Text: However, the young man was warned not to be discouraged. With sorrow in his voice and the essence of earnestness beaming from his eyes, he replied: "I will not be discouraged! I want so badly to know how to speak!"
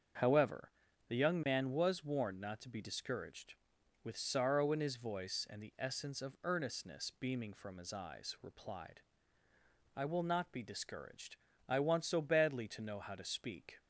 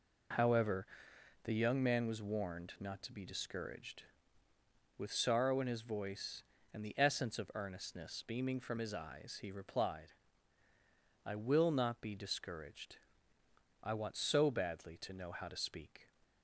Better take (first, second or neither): second